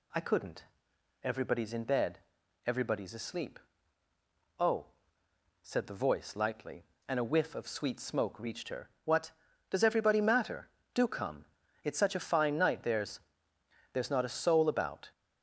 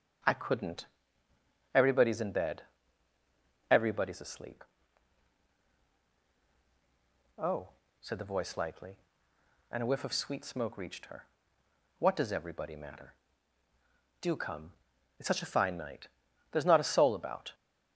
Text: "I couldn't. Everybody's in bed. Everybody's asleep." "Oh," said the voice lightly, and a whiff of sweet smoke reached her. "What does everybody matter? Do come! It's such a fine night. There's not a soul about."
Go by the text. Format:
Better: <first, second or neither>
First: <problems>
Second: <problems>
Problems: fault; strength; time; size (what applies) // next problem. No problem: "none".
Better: second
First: says "There's" twice; at 13.9 s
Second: none